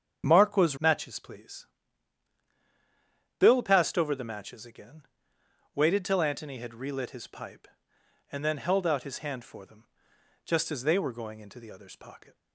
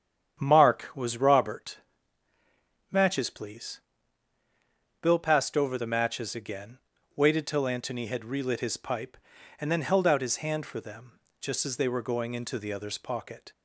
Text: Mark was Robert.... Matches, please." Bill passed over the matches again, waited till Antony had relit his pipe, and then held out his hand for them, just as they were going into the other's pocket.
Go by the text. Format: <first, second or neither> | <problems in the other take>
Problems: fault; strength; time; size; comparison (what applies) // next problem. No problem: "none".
second | starts louder than the rest; strong; until 1.2 s; 8 dB; strong in the second // skips "Robert"; at 0.7 s